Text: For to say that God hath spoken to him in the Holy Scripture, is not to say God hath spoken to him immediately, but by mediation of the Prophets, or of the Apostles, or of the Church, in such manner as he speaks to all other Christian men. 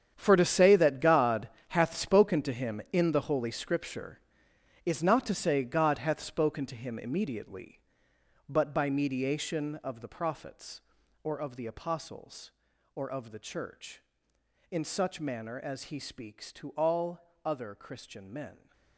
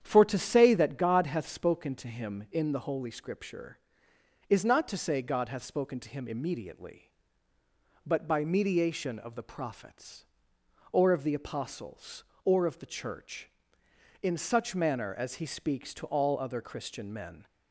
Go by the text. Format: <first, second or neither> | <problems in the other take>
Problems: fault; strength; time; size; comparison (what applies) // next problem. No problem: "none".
second | gets quieter; strong; throughout; 15 dB // starts louder than the rest; strong; until 1.1 s; 8.5 dB; strong in the second // pauses between "God" and "hath"; slight; at 1.4 s; 0.22 s long